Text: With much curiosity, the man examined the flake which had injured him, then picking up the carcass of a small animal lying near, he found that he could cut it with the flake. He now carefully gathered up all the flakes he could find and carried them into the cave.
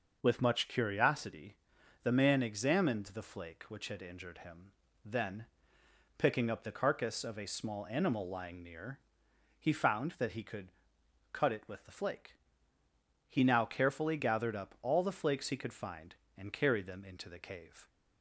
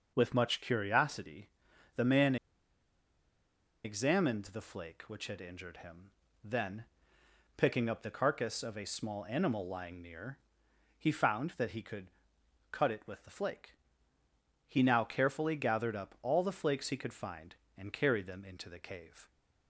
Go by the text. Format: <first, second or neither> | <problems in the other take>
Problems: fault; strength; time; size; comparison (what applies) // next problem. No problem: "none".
first | pauses between "man" and "examined"; strong; at 2.3 s; 1.4 s long // pauses between "then" and "picking"; noticeable; at 6.8 s; 0.72 s long; noticeable in the first // pauses between "could" and "cut"; noticeable; at 12.0 s; 0.64 s long; noticeable in the first